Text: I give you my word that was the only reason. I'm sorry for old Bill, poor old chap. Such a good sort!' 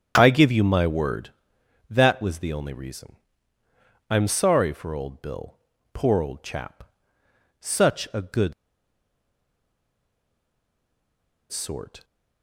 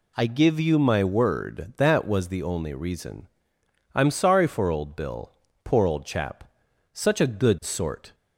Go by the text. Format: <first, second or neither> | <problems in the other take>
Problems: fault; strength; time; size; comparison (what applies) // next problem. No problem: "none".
second | starts louder than the rest; strong; until 1.1 s; 8 dB // pauses between "good" and "sort"; strong; at 8.5 s; 2.9 s long